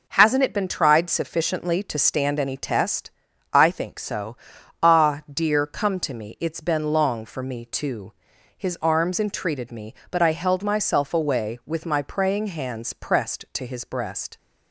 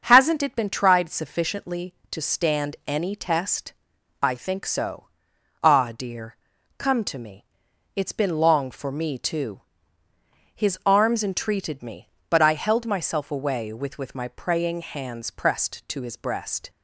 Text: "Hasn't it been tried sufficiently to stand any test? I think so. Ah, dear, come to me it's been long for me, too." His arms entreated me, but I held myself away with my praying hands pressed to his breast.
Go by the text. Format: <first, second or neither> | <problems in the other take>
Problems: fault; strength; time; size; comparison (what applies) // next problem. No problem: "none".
first | starts louder than the rest; until 1.0 s; 6.5 dB // pauses between "me" and "it's"; noticeable; at 7.4 s; 0.50 s long // says "with" twice; at 13.9 s